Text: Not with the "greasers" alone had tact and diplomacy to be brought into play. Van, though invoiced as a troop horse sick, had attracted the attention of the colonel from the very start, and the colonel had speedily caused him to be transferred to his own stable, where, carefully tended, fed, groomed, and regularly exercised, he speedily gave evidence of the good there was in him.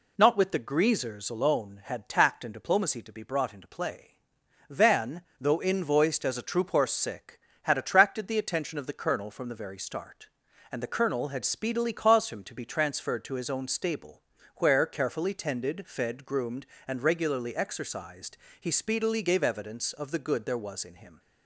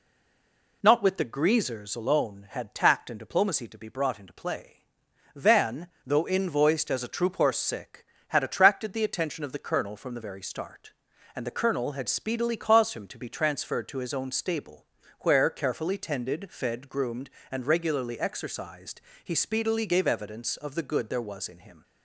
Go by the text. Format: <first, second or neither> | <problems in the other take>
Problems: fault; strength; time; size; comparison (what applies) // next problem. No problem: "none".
first | stays silent before the first word; slight; until 0.8 s; 0.8 s long